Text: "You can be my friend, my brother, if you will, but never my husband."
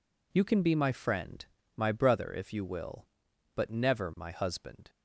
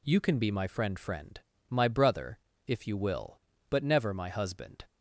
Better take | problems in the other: first | says "friend" twice; at 0.9 s

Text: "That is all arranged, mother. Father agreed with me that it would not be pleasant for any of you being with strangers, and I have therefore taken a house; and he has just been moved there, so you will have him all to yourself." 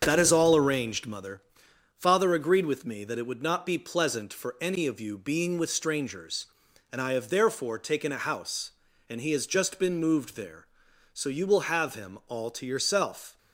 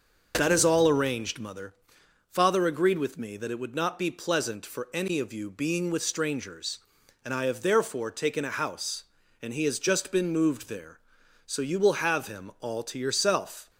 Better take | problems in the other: second | gets quieter; noticeable; throughout; 5 dB // starts louder than the rest; strong; until 1.0 s; 7.5 dB; also in the second

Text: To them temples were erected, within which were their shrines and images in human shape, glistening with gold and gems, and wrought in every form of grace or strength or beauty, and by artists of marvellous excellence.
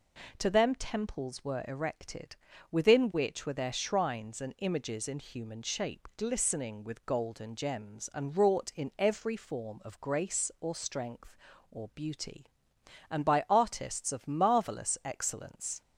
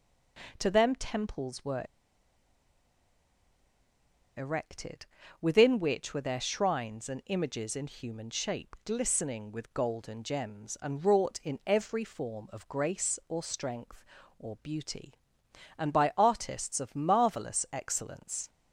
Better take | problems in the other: first | pauses between "were" and "erected"; strong; at 1.8 s; 2.5 s long

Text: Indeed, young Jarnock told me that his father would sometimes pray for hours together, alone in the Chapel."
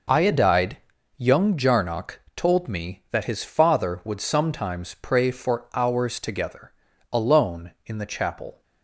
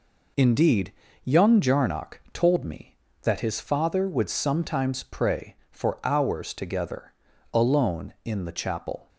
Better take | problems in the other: second | says "Iodide" for "Indeed"; at 0.1 s

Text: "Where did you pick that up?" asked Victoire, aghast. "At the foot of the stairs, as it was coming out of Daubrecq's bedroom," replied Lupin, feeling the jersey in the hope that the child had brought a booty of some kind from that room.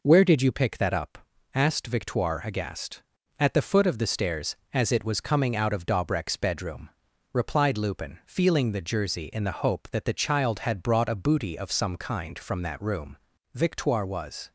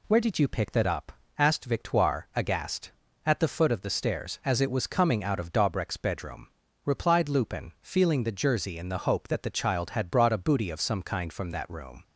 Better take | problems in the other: second | goes on to say "Victoire was"; noticeable; from 13.5 s on; 0.98 s long

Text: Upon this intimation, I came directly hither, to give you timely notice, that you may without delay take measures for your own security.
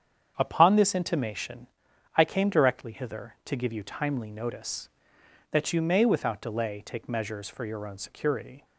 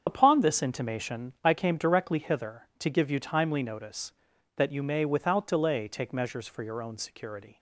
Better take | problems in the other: first | loses the start of "Upon"; at 0.0 s; 45 ms // starts louder than the rest; strong; until 1.0 s; 7.5 dB; strong in the first

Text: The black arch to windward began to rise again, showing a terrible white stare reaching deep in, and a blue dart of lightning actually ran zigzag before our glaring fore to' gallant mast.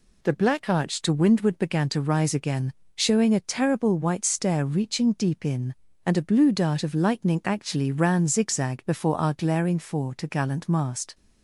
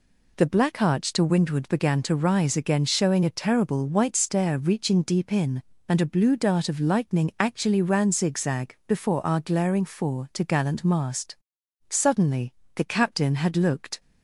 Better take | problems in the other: first | goes on to say "Suddenly the captain had looked"; strong; from 11.8 s on; 2.1 s long

